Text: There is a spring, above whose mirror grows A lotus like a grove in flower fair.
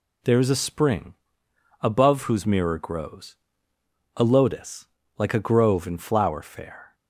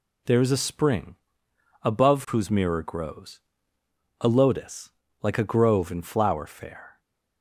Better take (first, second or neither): neither